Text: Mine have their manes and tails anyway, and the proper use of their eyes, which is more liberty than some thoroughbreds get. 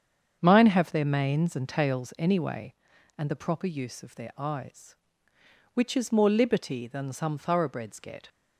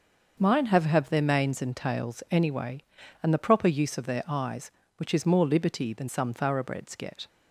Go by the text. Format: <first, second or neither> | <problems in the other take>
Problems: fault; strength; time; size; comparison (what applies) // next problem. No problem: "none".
first | starts louder than the rest; until 1.4 s; 6.5 dB; strong in the first // says "have" twice; at 0.8 s